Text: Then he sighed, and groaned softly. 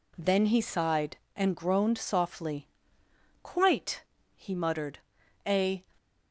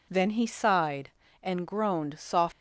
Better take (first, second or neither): second